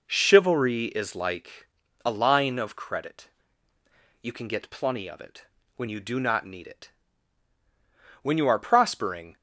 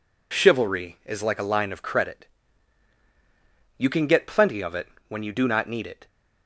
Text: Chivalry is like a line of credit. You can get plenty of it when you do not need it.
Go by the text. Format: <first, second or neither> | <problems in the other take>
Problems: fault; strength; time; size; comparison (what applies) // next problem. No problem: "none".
second | pauses between "like" and "a"; at 1.6 s; 0.38 s long // pauses between "it" and "when"; slight; at 5.4 s; 0.32 s long; slight in the second // goes on to say "When you are prospering"; noticeable; from 8.2 s on; 1.1 s long